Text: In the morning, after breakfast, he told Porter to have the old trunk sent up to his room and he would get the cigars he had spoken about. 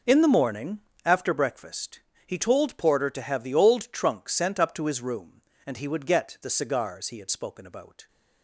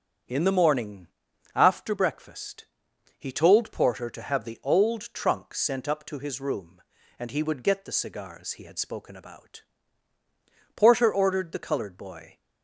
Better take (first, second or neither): first